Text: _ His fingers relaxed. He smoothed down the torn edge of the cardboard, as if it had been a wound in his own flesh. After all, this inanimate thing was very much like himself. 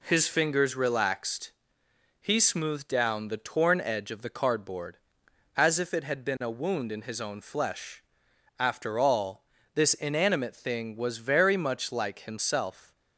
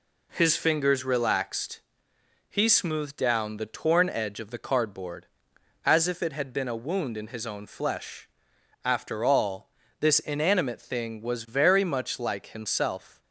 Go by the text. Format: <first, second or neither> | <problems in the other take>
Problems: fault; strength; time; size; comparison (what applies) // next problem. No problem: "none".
neither | none